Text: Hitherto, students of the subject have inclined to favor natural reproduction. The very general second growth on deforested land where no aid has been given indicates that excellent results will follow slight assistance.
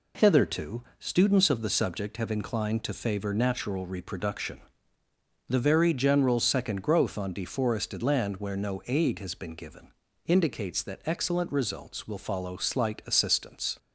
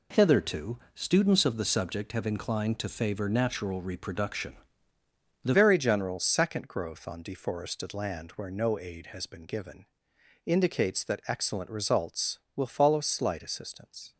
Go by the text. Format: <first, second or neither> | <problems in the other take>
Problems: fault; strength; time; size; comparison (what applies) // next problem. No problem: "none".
first | changes voice at "very"; from 5.5 s on; 8.6 s long // pauses between "given" and "indicates"; noticeable; at 9.8 s; 0.62 s long; slight in the first